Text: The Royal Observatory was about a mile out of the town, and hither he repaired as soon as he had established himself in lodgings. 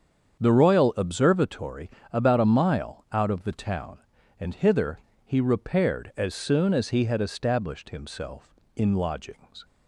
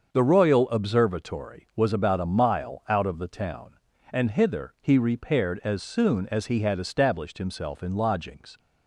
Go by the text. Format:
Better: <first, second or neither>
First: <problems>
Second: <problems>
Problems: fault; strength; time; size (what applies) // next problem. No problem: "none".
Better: second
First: starts louder than the rest; strong; until 1.4 s; 7.5 dB // skips "was"; at 1.9 s // pauses between "hither" and "he"; slight; at 4.9 s; 0.26 s long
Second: starts louder than the rest; until 1.1 s; 6.5 dB